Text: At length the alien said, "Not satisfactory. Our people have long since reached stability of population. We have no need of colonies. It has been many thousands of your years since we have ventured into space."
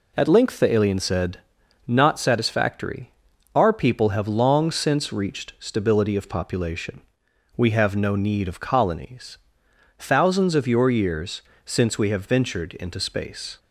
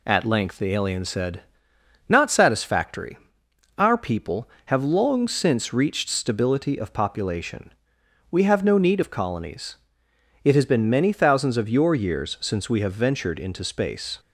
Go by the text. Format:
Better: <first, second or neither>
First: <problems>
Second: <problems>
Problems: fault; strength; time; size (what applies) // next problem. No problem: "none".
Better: second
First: skips "It has been many"; at 9.6 s // pauses between "years" and "since"; slight; at 11.4 s; 0.22 s long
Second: none